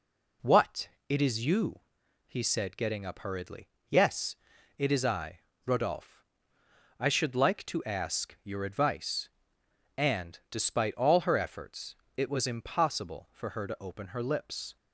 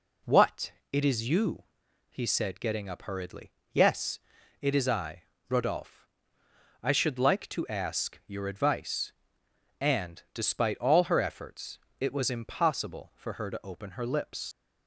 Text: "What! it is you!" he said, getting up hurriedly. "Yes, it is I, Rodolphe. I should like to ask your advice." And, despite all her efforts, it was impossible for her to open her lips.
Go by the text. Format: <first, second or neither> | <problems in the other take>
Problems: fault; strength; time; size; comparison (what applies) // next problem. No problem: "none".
first | leaves "lips" unfinished; at 14.5 s; 75 ms